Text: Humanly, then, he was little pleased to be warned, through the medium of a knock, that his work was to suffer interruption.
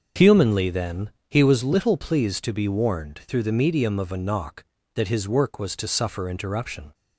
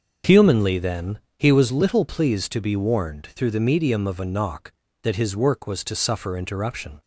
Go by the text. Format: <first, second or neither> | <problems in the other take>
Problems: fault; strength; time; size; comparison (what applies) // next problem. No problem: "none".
neither | starts louder than the rest; the same in both